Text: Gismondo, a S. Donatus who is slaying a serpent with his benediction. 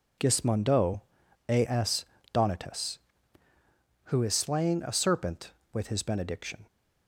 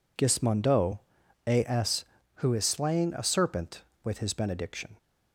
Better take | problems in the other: first | skips "Donatus"; at 2.2 s

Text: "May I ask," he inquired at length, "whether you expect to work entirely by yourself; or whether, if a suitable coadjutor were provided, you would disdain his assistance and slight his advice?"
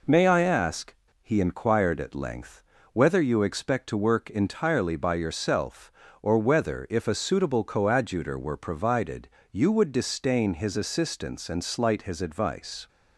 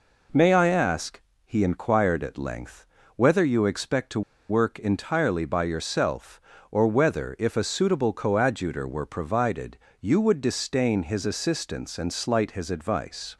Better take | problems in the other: first | pauses between "to" and "work"; slight; at 4.2 s; 0.28 s long

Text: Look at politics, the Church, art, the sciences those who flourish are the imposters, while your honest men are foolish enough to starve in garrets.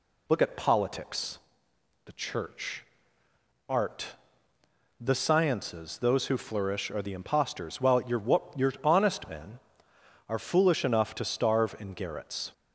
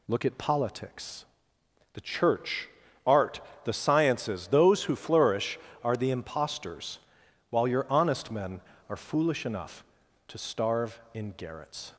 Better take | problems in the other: second | says "your" twice; at 8.5 s

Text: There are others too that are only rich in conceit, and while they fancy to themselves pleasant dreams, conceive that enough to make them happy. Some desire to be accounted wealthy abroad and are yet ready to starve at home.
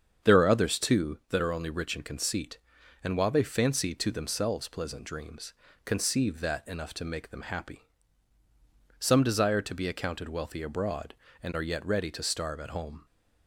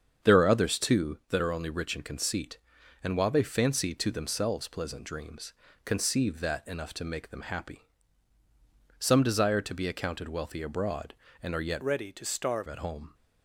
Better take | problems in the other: first | starts louder than the rest; strong; until 1.3 s; 7.5 dB; strong in the first // changes voice from "ready" to "starve"; from 11.8 to 12.6 s; 0.8 s long

